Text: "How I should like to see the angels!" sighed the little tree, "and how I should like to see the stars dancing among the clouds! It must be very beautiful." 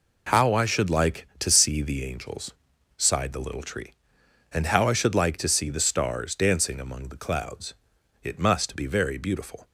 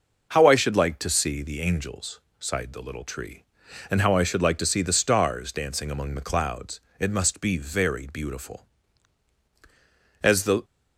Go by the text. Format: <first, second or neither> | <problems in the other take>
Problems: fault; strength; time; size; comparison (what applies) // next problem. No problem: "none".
first | goes on to say "As the"; slight; from 10.2 s on; 0.42 s long